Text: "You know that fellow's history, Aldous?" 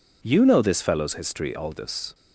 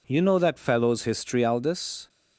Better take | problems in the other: second | says "this" for "that"; at 0.6 s

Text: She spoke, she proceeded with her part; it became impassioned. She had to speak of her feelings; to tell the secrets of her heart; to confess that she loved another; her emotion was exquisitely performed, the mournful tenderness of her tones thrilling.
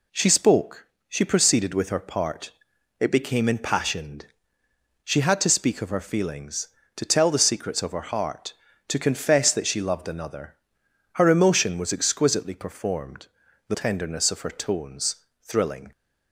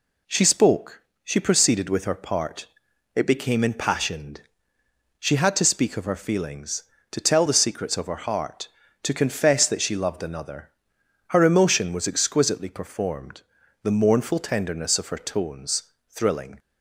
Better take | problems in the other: second | skips "mournful"; at 13.7 s // pauses between "tones" and "thrilling"; slight; at 15.1 s; 0.26 s long; slight in the second

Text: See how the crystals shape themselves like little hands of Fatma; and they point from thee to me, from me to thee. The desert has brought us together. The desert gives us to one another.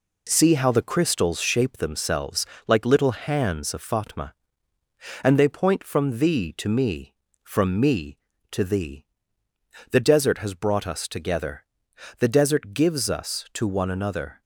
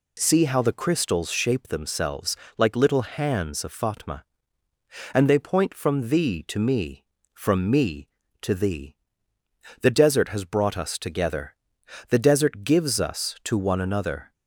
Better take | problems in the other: second | gets quieter; noticeable; throughout; 4.5 dB // pauses between "themselves" and "like"; slight; at 2.4 s; 0.20 s long; slight in the second

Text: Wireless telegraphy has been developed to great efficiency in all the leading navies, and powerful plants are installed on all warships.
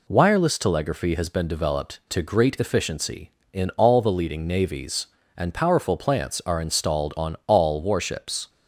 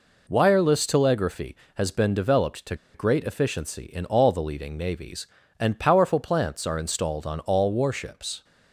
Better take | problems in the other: first | pauses between "to" and "great"; slight; at 2.7 s; 0.19 s long

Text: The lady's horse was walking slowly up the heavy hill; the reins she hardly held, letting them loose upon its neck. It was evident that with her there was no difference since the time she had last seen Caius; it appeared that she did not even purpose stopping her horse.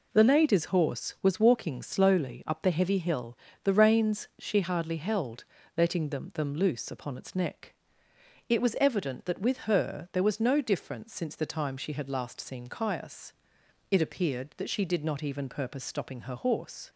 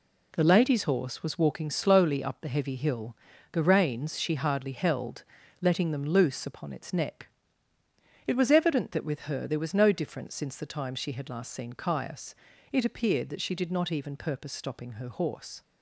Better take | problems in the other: second | says "them" twice; at 6.3 s

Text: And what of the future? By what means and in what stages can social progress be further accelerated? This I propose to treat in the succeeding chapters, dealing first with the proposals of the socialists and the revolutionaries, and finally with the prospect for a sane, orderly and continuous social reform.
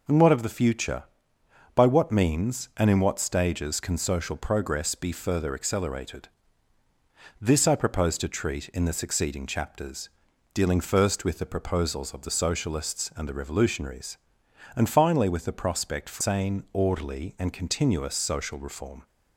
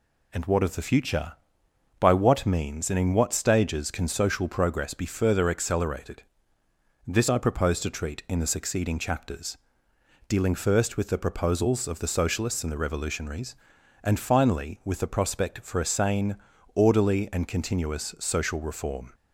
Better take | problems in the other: second | skips "a"; at 16.2 s

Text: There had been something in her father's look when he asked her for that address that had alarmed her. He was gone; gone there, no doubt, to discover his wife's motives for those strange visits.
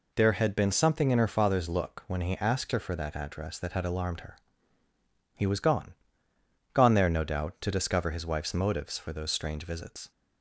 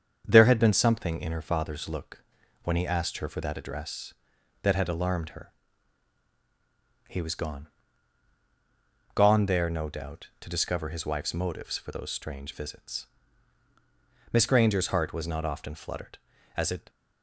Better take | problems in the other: first | starts louder than the rest; strong; until 1.2 s; 7.5 dB // pauses between "look" and "when"; at 2.2 s; 0.40 s long // goes on to say "Miss Granger's heart was not often fluttered as it"; strong; from 14.3 s on; 2.5 s long

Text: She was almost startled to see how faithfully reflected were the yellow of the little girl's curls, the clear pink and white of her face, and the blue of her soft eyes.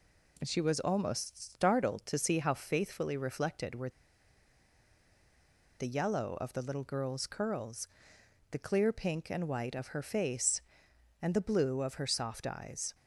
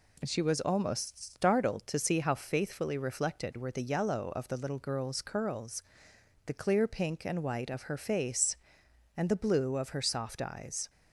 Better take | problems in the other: second | pauses between "were" and "the"; strong; at 3.8 s; 1.8 s long

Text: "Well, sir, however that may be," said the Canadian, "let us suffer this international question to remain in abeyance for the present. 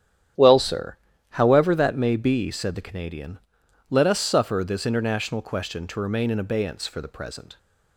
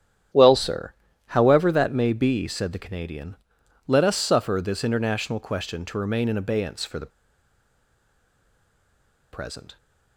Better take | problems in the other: first | starts louder than the rest; strong; until 1.6 s; 10 dB; strong in the first // pauses between "the" and "present"; strong; at 7.1 s; 2.2 s long

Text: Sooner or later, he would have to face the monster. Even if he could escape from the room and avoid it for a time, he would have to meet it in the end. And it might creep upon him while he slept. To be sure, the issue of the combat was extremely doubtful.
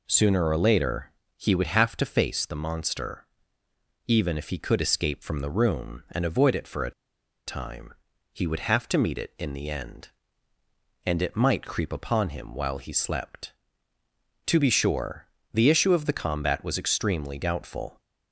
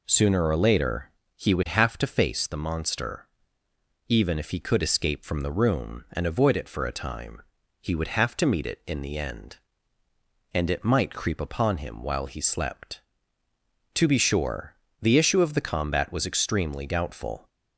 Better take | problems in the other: second | pauses between "a" and "time"; noticeable; at 6.9 s; 0.55 s long

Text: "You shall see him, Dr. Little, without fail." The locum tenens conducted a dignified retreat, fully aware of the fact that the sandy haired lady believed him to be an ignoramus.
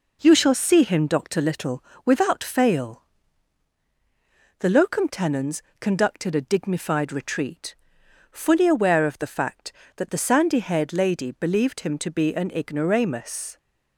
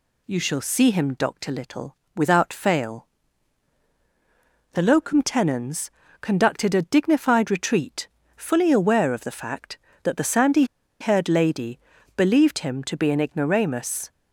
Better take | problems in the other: first | pauses between "tenens" and "conducted"; slight; at 5.8 s; 0.32 s long; slight in the first // pauses between "sandy" and "haired"; at 10.6 s; 0.36 s long // pauses between "lady" and "believed"; slight; at 11.7 s; 0.36 s long

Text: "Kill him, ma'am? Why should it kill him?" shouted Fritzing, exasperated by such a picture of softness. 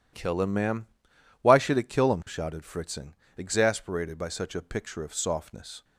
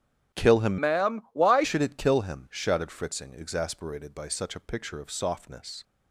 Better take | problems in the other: first | starts louder than the rest; strong; until 1.4 s; 10.5 dB // changes voice from "ma'am" to "Why"; from 0.8 to 1.6 s; 0.8 s long

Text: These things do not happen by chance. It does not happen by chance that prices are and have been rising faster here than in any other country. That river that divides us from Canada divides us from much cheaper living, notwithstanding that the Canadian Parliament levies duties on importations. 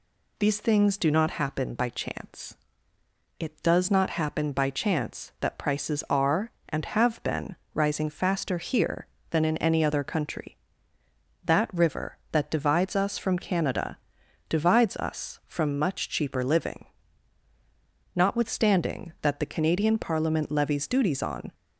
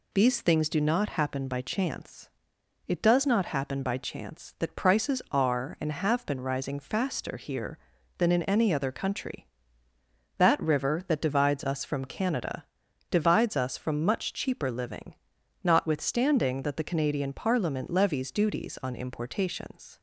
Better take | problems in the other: second | pauses between "been" and "rising"; slight; at 7.5 s; 0.18 s long // pauses between "Canada" and "divides"; noticeable; at 13.9 s; 0.50 s long; noticeable in the second // stops before "importations"; at 21.5 s

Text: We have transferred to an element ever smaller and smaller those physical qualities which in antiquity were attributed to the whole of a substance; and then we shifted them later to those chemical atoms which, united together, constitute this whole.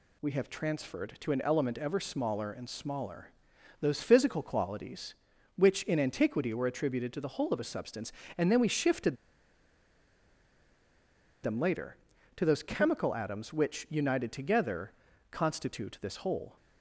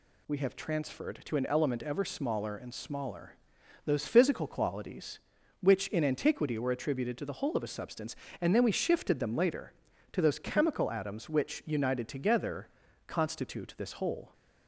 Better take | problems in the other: second | pauses between "smaller" and "those"; noticeable; at 3.3 s; 0.50 s long; noticeable in the second // pauses between "shifted" and "them"; strong; at 9.1 s; 2.2 s long

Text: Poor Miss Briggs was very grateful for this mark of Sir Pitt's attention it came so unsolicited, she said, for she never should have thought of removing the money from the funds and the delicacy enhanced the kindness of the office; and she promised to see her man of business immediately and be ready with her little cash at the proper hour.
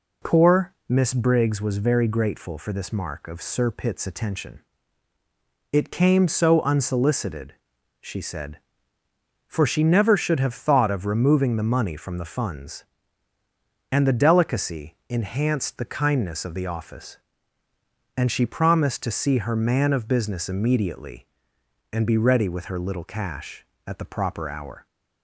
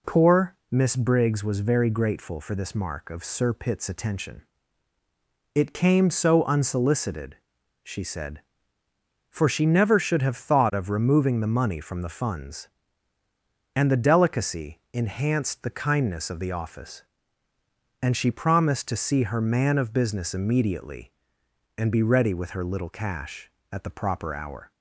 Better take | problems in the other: neither | pauses between "attention" and "it"; the same in both

